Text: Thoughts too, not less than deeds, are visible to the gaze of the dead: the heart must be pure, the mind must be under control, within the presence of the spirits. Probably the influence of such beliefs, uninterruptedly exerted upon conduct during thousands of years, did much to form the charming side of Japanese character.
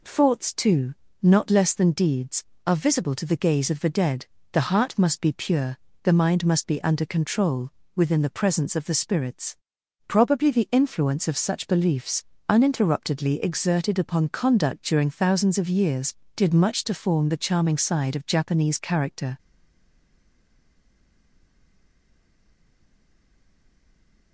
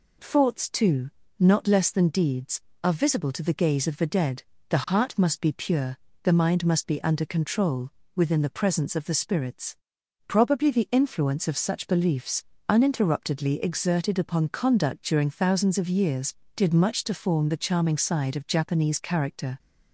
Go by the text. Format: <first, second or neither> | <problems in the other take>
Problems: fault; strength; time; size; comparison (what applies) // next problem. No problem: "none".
second | stays silent after the last word; strong; from 19.3 s on; 5.0 s long